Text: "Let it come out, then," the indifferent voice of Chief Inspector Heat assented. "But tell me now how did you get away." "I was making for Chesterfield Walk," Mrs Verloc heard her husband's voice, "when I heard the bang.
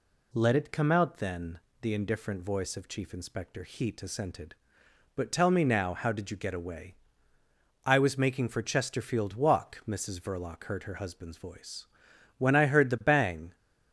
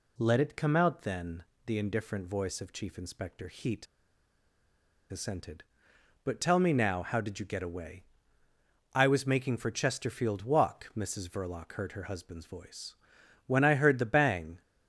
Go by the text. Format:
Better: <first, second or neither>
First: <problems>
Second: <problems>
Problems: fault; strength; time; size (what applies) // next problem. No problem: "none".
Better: first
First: none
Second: pauses between "Heat" and "assented"; strong; at 3.8 s; 1.2 s long